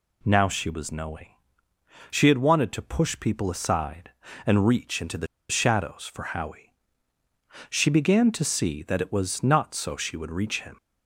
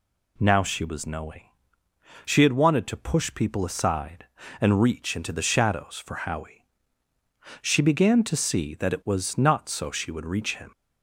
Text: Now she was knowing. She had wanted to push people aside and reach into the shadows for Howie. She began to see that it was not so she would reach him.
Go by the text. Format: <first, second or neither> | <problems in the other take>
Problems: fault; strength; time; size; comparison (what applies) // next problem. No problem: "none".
second | pauses between "the" and "shadows"; slight; at 5.2 s; 0.24 s long